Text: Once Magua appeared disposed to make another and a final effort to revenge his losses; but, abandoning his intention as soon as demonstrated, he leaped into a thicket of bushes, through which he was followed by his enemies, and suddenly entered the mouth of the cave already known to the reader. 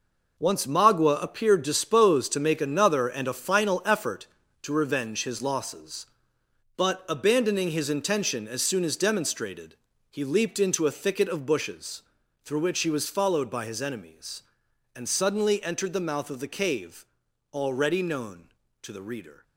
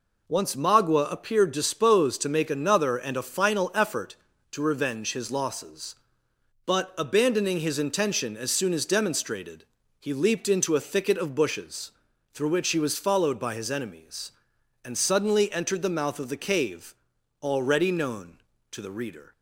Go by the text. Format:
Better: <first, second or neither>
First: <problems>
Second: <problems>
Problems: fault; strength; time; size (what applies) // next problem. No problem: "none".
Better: second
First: gets quieter; strong; throughout; 10 dB // pauses between "cave" and "already"; at 17.0 s; 0.44 s long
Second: pauses between "cave" and "already"; at 16.9 s; 0.44 s long